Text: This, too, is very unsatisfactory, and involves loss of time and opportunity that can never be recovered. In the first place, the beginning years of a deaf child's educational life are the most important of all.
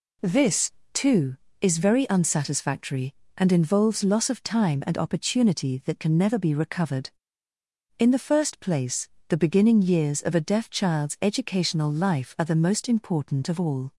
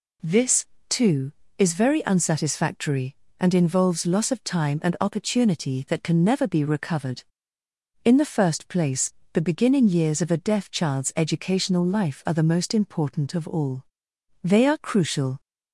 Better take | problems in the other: first | goes on to say "They are crucial"; noticeable; from 14.4 s on; 0.98 s long

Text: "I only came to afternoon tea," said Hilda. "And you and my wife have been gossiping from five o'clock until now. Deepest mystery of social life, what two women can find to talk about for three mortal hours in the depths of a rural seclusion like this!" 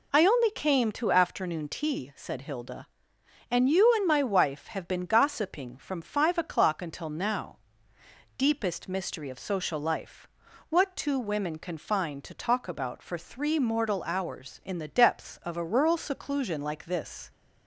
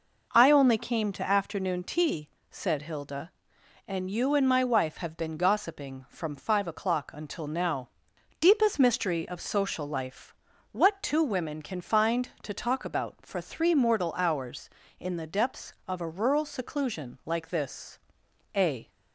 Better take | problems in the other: first | goes on to say "A"; slight; from 18.5 s on; 0.36 s long

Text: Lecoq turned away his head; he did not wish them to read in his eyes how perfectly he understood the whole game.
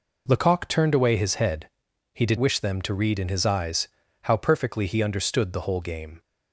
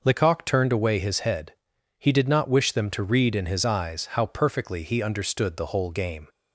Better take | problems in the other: second | skips "not"; at 2.3 s // pauses between "eyes" and "how"; slight; at 3.8 s; 0.34 s long

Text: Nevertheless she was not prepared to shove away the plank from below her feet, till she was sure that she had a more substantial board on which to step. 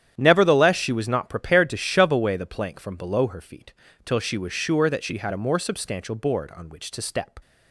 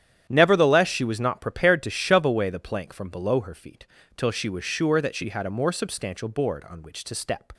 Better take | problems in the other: neither | starts louder than the rest; strong; the same in both

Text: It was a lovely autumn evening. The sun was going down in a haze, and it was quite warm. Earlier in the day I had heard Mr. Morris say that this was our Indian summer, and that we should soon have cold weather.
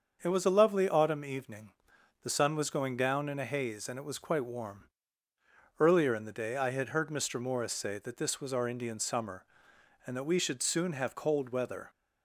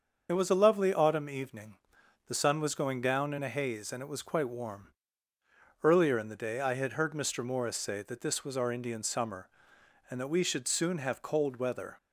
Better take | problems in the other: first | loses the start of "It"; at 0.2 s; 40 ms // starts louder than the rest; until 1.3 s; 6.5 dB; also in the first

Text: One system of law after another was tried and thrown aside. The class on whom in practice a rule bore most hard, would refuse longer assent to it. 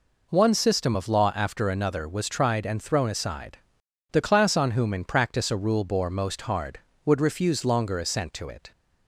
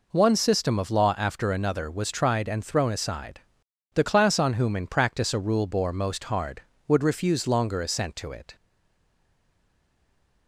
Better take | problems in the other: first | stays silent after the last word; noticeable; from 8.5 s on; 1.9 s long

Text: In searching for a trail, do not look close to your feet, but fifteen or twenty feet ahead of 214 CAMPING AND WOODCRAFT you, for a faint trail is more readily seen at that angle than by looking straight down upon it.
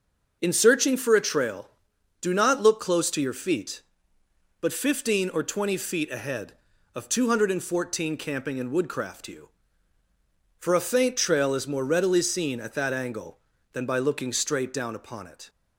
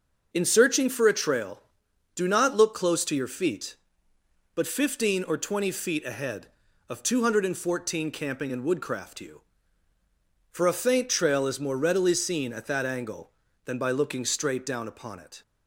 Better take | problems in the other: neither | starts louder than the rest; the same in both

